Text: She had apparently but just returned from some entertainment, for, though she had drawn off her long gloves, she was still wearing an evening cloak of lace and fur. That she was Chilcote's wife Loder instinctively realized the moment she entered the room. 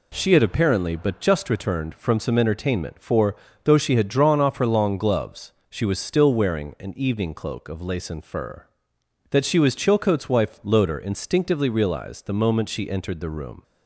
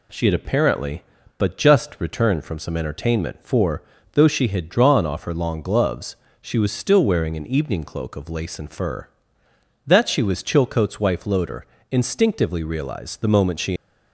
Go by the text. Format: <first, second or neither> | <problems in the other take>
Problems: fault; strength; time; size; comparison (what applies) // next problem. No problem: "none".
first | pauses between "Loder" and "instinctively"; slight; at 11.6 s; 0.26 s long // stops before "entered the room"; at 13.7 s